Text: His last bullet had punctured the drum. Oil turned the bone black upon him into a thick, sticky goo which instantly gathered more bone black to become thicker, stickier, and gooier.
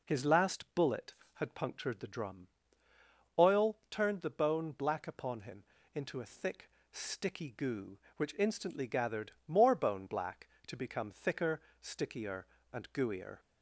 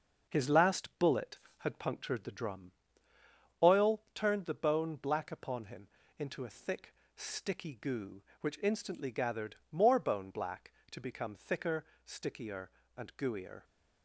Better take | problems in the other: first | gets quieter; noticeable; throughout; 6 dB // pauses between "him" and "into"; slight; at 5.8 s; 0.32 s long; slight in the first // pauses between "gathered" and "more"; slight; at 9.5 s; 0.16 s long; slight in the first

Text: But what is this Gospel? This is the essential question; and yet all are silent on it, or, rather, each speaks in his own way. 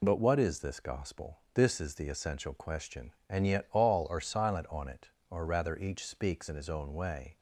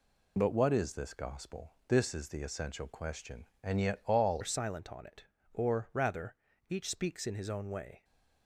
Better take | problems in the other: first | changes voice at "are"; from 4.4 s on; 3.6 s long

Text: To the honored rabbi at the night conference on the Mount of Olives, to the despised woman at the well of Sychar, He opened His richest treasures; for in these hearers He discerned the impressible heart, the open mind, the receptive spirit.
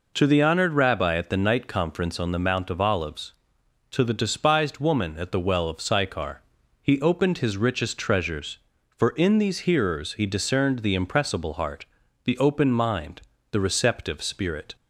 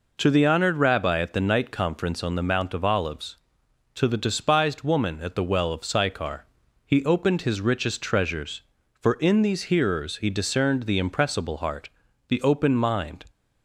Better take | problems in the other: first | stops before "the receptive spirit"; at 13.2 s

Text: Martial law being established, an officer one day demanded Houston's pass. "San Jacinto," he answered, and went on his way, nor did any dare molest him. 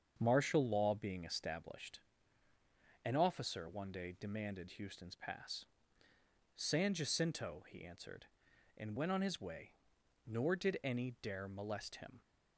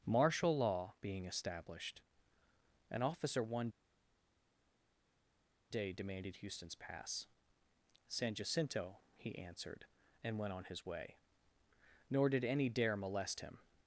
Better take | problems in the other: first | starts louder than the rest; until 1.1 s; 7 dB; also in the first // pauses between "one" and "day"; strong; at 3.6 s; 2.0 s long

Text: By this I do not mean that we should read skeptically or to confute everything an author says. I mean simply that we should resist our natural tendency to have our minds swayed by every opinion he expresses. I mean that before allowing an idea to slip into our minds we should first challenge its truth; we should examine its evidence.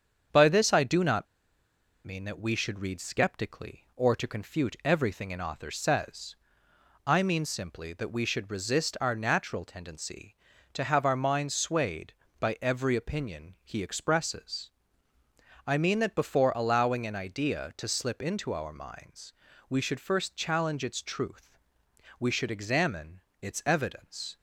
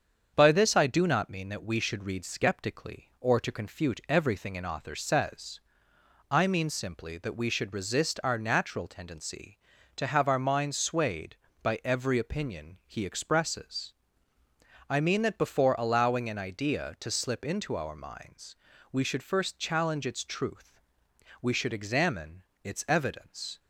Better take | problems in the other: second | starts louder than the rest; strong; until 2.1 s; 7.5 dB; strong in the second // pauses between "not" and "mean"; noticeable; at 1.2 s; 0.79 s long // pauses between "minds" and "we"; slight; at 19.3 s; 0.34 s long; slight in the second // pauses between "examine" and "its"; slight; at 23.2 s; 0.20 s long; slight in the second

